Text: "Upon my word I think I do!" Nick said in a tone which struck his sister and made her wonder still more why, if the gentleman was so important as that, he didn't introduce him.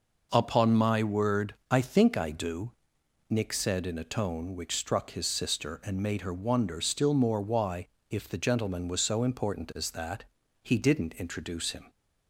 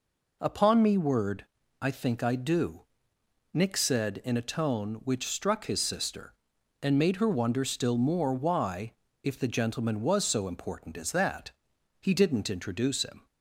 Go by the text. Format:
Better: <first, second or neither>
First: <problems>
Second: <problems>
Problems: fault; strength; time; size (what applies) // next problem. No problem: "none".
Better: first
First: pauses between "word" and "I"; slight; at 1.5 s; 0.18 s long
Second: says "me" for "my"; at 0.8 s // pauses between "word" and "I"; slight; at 1.4 s; 0.36 s long